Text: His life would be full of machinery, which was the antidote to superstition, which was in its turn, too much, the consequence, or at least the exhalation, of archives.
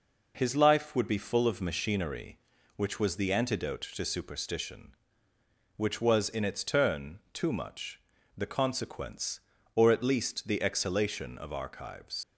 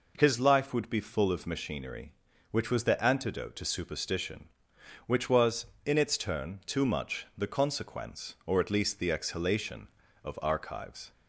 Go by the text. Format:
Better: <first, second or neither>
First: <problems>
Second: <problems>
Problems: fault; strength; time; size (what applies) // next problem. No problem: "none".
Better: second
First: leaves "archives" unfinished; at 12.2 s; 85 ms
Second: none